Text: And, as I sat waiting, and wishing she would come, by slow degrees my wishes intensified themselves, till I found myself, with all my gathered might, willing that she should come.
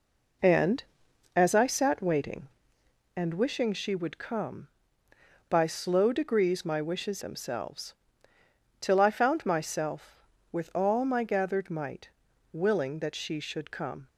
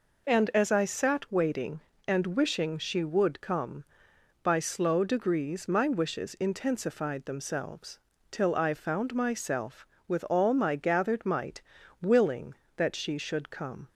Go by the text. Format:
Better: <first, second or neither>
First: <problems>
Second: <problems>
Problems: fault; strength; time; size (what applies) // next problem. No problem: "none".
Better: second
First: skips "intensified"; at 7.2 s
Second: none